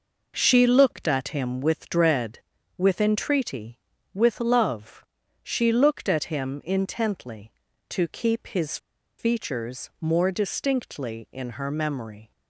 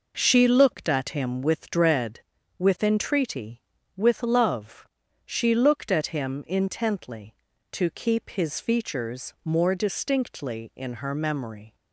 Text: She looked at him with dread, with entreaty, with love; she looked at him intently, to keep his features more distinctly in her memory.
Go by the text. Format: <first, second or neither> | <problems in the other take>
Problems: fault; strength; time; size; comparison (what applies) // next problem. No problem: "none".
second | pauses between "his" and "features"; at 8.7 s; 0.41 s long